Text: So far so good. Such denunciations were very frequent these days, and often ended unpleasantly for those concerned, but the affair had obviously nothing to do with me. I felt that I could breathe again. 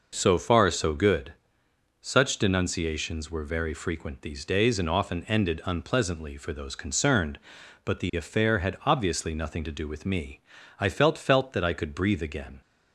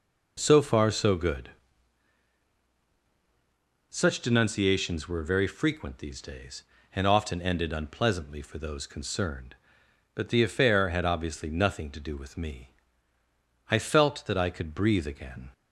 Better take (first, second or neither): second